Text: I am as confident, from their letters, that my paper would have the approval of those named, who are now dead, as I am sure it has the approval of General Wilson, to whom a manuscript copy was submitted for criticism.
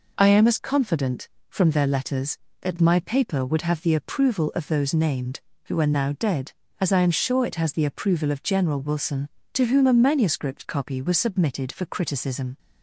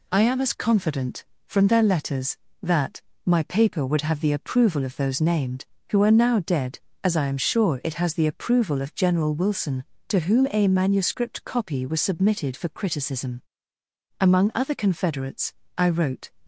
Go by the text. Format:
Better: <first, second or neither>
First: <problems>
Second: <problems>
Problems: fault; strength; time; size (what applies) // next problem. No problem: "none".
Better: first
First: none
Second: pauses between "that" and "my"; slight; at 3.0 s; 0.24 s long // goes on to say "Among other Confederates I wrote"; strong; from 14.1 s on; 2.1 s long